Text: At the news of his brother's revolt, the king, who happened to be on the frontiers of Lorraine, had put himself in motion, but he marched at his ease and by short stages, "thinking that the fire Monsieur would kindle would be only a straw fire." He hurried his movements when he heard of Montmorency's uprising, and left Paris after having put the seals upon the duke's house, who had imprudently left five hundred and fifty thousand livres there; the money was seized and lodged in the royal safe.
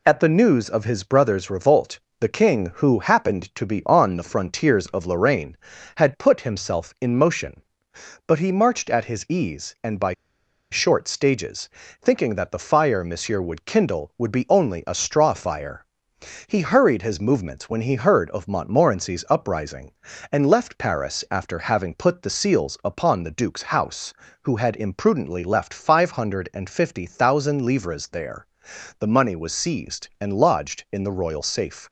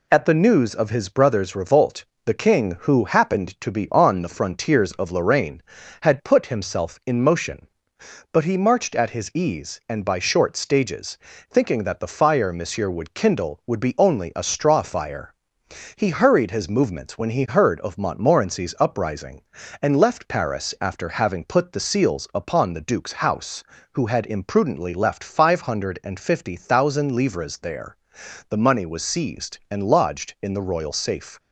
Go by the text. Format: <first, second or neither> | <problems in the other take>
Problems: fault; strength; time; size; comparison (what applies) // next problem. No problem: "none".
second | pauses between "by" and "short"; noticeable; at 10.1 s; 0.59 s long